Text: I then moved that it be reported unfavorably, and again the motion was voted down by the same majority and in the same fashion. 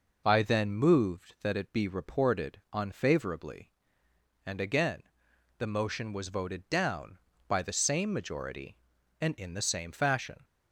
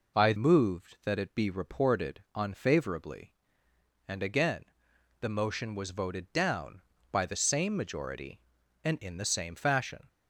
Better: first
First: pauses between "again" and "the"; noticeable; at 5.0 s; 0.56 s long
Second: skips "then"; at 0.3 s // pauses between "again" and "the"; noticeable; at 4.6 s; 0.56 s long

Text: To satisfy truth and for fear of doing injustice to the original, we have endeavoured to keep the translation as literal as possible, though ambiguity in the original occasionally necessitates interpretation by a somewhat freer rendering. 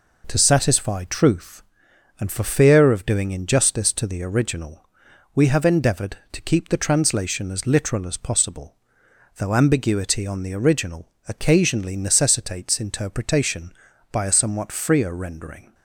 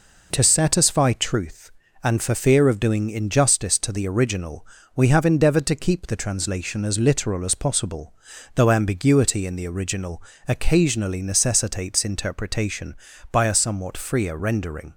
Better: second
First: says "on" for "in"; at 10.2 s // pauses between "original" and "occasionally"; slight; at 11.0 s; 0.20 s long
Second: pauses between "original" and "occasionally"; slight; at 10.2 s; 0.24 s long

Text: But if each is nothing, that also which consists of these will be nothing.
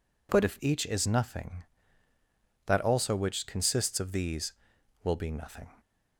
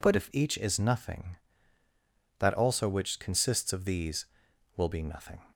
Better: neither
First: none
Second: none

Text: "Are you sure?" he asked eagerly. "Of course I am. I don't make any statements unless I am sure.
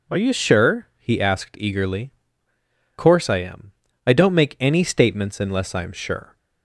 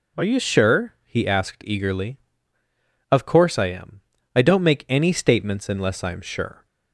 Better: second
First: skips "Of"; at 2.5 s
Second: none

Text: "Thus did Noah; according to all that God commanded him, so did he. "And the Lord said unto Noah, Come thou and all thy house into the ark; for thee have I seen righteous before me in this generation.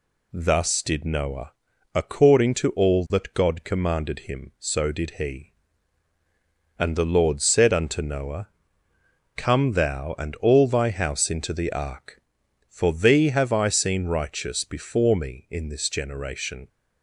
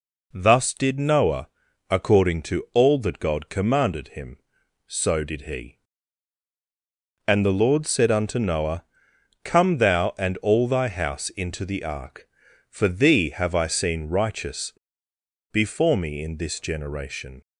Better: first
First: none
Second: pauses between "righteous" and "before"; noticeable; at 14.7 s; 0.80 s long

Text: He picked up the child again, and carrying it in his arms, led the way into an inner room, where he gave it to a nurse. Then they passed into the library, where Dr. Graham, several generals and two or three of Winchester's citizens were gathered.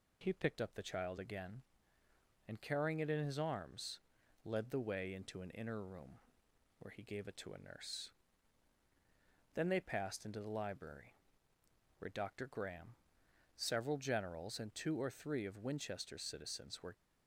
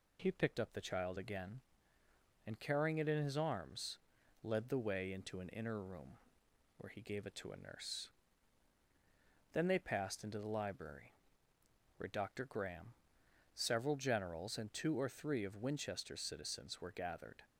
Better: second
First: stops before "gathered"; at 16.9 s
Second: none

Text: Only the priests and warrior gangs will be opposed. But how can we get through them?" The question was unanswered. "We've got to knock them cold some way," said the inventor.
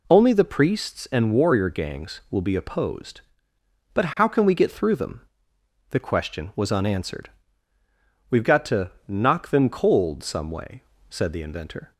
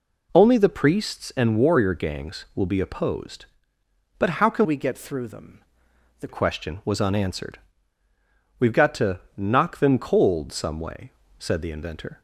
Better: first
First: pauses between "to" and "knock"; slight; at 8.9 s; 0.16 s long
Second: changes voice from "we" to "The"; from 4.6 to 6.2 s; 1.6 s long // pauses between "to" and "knock"; slight; at 9.1 s; 0.16 s long

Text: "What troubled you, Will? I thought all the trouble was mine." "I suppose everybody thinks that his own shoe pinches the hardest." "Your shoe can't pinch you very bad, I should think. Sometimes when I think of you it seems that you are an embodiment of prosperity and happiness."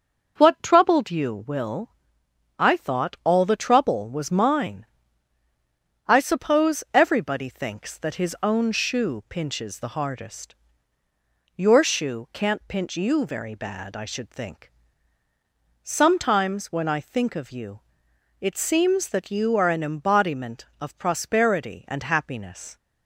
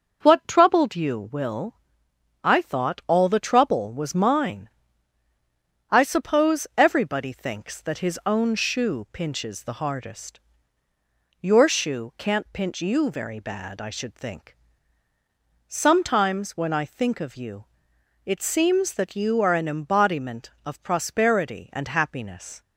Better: neither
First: starts louder than the rest; until 1.3 s; 6.5 dB // pauses between "you" and "it"; noticeable; at 17.7 s; 0.60 s long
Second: starts louder than the rest; until 1.2 s; 6.5 dB // pauses between "you" and "it"; noticeable; at 17.6 s; 0.60 s long

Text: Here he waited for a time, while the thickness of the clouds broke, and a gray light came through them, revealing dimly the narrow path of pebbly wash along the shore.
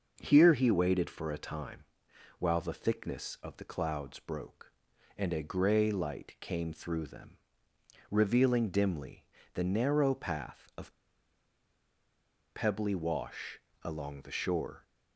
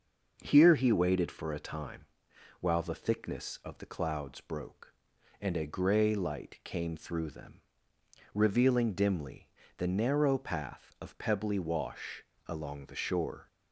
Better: second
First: starts louder than the rest; noticeable; until 1.2 s; 6 dB // pauses between "dimly" and "the"; slight; at 9.2 s; 0.28 s long // pauses between "of" and "pebbly"; strong; at 10.9 s; 1.6 s long // pauses between "wash" and "along"; slight; at 13.5 s; 0.24 s long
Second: starts louder than the rest; noticeable; until 1.4 s; 6 dB // pauses between "dimly" and "the"; slight; at 9.4 s; 0.28 s long // pauses between "wash" and "along"; slight; at 12.2 s; 0.24 s long

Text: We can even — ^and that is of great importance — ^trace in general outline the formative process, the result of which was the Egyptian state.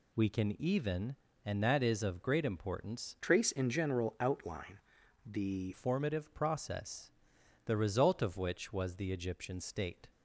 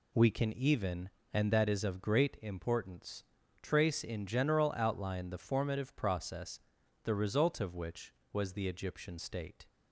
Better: second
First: changes voice from "trace" to "the"; from 3.2 to 5.7 s; 2.5 s long // pauses between "outline" and "the"; noticeable; at 4.7 s; 0.46 s long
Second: none

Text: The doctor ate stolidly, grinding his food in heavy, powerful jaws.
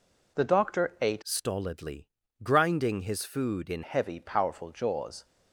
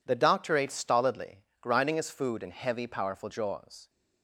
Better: second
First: changes voice from "stolidly" to "in"; from 1.2 to 3.8 s; 2.6 s long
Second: none

